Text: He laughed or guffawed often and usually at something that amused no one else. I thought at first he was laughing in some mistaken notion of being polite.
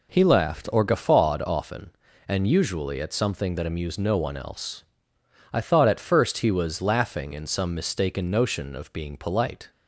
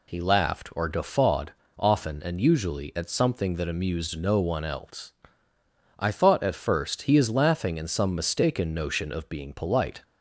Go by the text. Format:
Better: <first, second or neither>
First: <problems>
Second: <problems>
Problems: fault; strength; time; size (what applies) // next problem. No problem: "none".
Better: first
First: none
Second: pauses between "guffawed" and "often"; slight; at 1.5 s; 0.26 s long // says "is" for "was"; at 7.1 s